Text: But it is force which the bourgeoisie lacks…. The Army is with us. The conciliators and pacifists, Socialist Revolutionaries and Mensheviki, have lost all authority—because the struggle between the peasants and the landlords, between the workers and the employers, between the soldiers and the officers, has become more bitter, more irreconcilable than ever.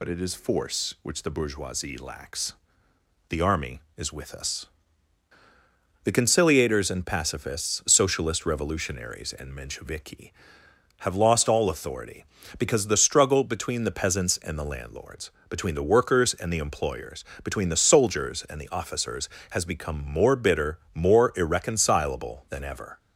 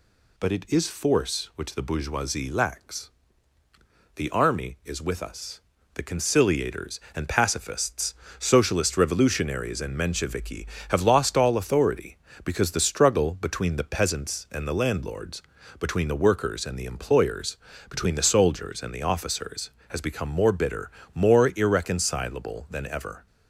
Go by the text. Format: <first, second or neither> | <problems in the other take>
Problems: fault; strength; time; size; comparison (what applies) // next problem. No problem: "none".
second | loses the start of "But"; at 0.0 s; 60 ms